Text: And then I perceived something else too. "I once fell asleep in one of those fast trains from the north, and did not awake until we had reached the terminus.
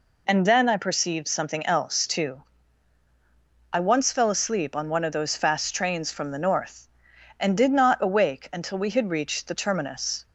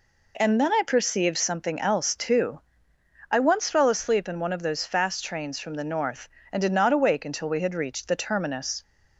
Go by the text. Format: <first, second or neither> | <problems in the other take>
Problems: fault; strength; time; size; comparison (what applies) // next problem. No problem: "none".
second | says "on" for "in"; at 4.7 s